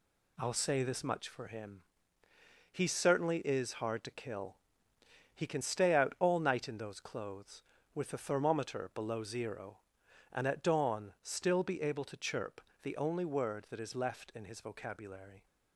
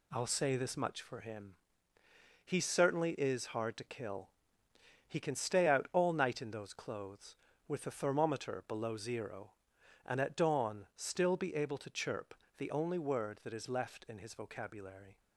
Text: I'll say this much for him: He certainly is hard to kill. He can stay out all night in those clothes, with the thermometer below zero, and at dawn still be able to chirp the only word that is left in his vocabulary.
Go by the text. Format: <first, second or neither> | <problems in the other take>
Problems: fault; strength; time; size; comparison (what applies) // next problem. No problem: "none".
neither | pauses between "chirp" and "the"; slight; the same in both